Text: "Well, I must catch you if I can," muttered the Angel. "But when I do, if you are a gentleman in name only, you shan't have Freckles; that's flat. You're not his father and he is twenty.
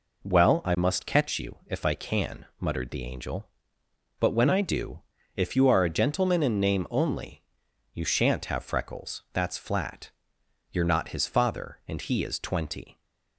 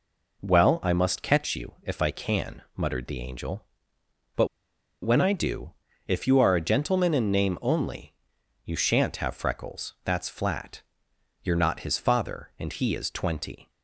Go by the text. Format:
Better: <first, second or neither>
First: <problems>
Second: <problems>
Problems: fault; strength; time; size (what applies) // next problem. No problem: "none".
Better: first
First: none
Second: pauses between "But" and "when"; noticeable; at 4.4 s; 0.55 s long